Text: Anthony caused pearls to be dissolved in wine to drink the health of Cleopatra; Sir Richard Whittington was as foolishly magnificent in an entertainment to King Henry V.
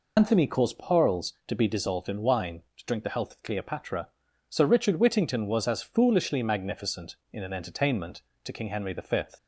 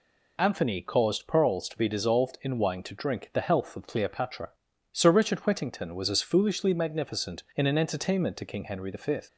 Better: second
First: loses the start of "Anthony"; at 0.1 s; 90 ms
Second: none

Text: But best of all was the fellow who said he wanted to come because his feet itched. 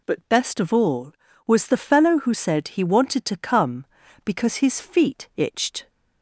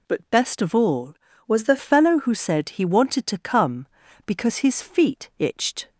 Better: first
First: none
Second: changes voice from "was" to "the"; from 1.4 to 1.7 s; 0.3 s long

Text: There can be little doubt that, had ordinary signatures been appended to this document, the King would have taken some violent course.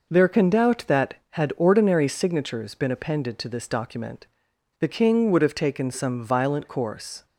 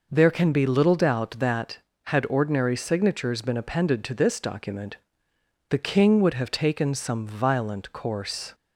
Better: second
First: skips "be little"; at 0.4 s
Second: none

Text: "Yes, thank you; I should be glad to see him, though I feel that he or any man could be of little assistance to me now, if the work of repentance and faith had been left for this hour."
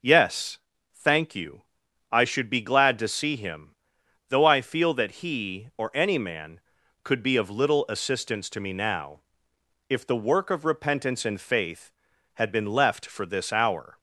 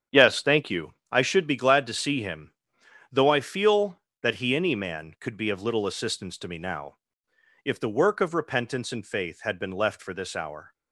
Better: first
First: none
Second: starts louder than the rest; strong; until 1.2 s; 8.5 dB // skips "or"; at 4.5 s

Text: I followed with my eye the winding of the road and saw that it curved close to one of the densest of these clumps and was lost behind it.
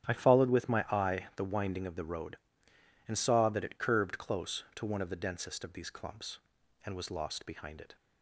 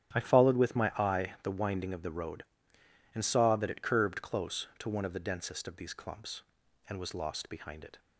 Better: neither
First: starts louder than the rest; strong; until 1.1 s; 11.5 dB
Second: starts louder than the rest; strong; until 1.2 s; 11.5 dB

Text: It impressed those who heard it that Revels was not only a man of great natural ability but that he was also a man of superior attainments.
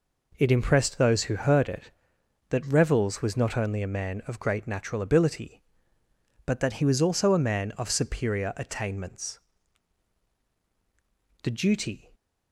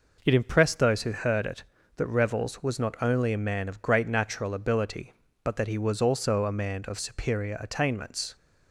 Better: second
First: goes on to say "The duty"; noticeable; from 11.4 s on; 0.66 s long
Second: none

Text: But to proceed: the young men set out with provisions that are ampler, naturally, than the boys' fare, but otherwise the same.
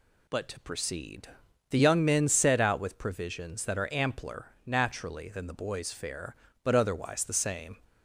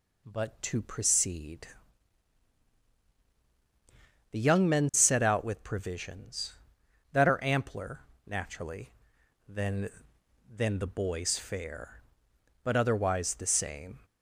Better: first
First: none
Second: says "than" twice; at 10.4 s

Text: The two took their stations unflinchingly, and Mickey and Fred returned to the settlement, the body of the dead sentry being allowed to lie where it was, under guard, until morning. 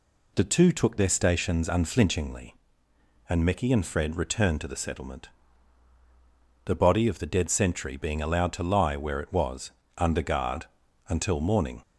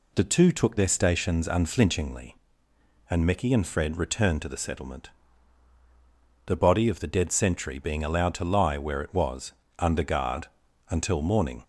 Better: neither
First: none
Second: none

